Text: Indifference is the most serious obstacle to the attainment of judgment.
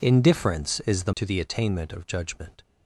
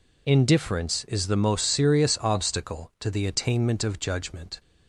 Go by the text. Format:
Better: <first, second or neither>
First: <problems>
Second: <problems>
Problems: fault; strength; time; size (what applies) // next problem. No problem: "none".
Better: second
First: skips "most serious obstacle"; at 1.1 s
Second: none